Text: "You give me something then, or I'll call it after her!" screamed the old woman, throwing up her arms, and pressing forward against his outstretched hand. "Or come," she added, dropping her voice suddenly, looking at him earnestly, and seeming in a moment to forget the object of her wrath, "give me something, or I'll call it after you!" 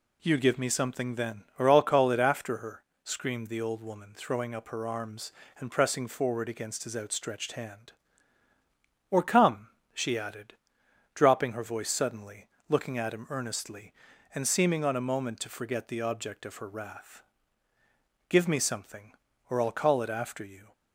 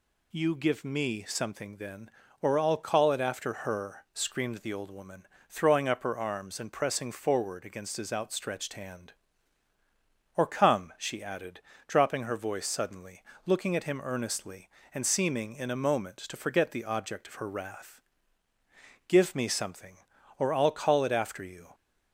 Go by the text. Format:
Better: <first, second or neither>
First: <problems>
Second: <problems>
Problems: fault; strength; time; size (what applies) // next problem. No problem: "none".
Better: second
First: says "on" for "in"; at 14.8 s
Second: none